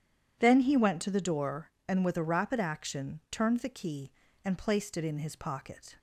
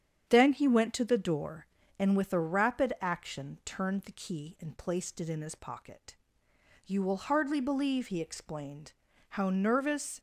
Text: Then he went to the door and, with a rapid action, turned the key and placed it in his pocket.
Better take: first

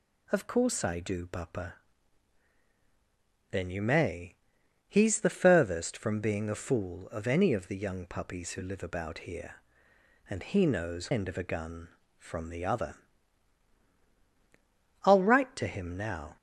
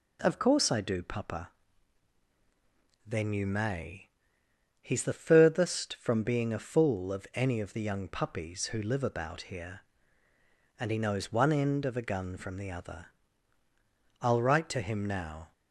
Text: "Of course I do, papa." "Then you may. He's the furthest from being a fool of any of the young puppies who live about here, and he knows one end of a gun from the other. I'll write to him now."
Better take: second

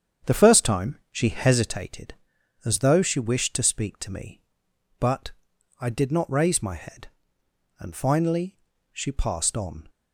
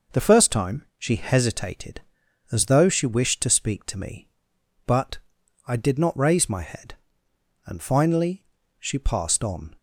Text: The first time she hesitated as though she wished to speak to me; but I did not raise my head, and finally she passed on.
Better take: second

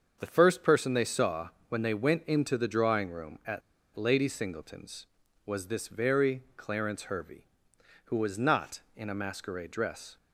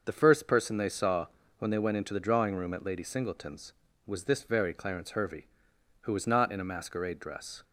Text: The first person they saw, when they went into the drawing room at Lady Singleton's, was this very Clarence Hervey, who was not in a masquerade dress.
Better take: second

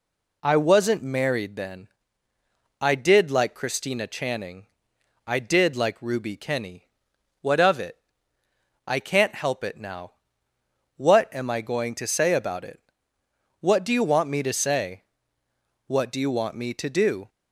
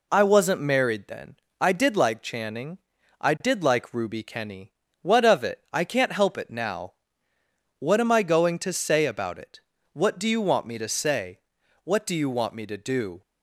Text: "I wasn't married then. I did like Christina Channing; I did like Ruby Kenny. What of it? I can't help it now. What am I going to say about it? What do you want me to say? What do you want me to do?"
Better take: first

